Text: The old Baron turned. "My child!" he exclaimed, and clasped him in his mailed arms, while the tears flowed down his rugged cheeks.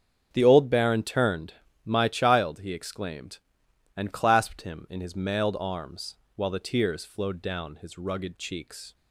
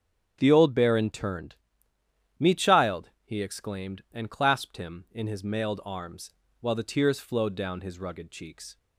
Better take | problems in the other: first | starts louder than the rest; strong; until 1.4 s; 8.5 dB; strong in the first // says "Me" for "My"; at 2.3 s

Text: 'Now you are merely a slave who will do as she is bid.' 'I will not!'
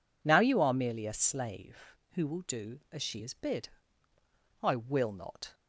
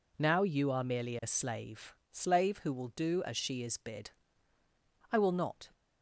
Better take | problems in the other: first | says "slave" twice; at 2.1 s

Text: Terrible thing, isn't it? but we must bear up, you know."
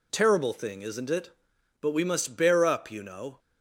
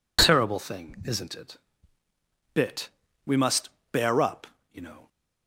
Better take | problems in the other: first | says "bit" for "but"; at 2.5 s // pauses between "must" and "bear"; slight; at 3.6 s; 0.24 s long

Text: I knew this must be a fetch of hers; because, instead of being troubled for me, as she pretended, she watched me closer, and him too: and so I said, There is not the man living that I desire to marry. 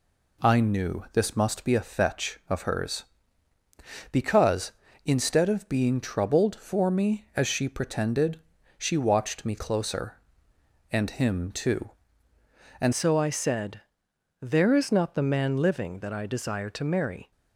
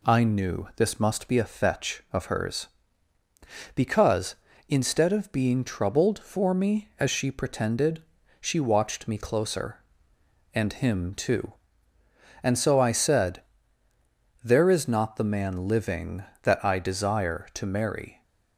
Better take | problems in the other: second | changes voice at "so"; from 12.9 s on; 4.4 s long

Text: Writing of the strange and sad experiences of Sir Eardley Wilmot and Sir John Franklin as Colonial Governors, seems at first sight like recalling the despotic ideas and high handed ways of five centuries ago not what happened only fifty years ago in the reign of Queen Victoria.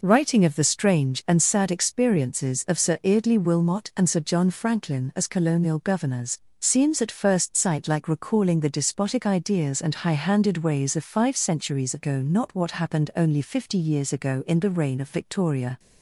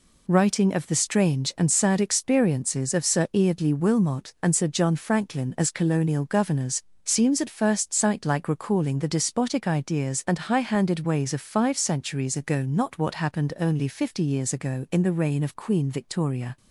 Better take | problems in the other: second | skips "Queen"; at 15.0 s

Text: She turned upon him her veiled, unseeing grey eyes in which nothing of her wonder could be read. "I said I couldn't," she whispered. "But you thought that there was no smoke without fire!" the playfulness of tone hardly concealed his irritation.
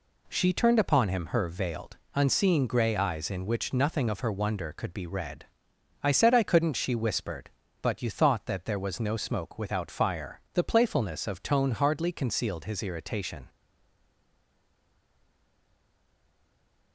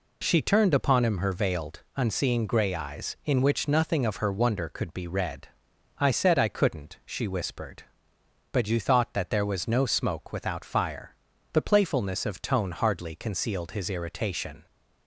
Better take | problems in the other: second | stays silent after the last word; strong; from 13.4 s on; 3.5 s long

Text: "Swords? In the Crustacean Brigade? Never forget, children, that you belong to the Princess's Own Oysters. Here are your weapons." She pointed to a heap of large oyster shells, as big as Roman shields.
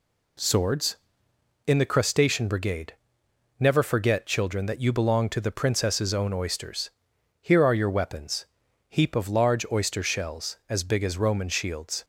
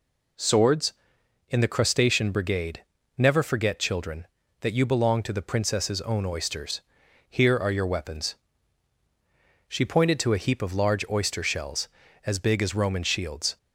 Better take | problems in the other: second | skips "She pointed to a"; at 8.6 s

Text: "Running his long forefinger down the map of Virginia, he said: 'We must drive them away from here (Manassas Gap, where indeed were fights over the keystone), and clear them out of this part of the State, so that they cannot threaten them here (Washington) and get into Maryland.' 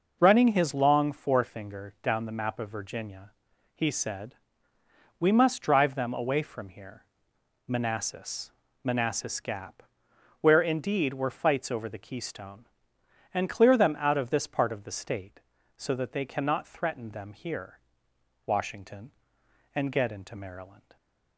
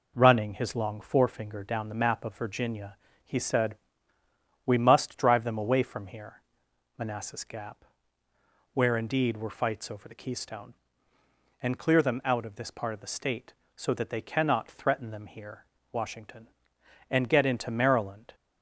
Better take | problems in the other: second | says "Manassas" twice; at 8.8 s

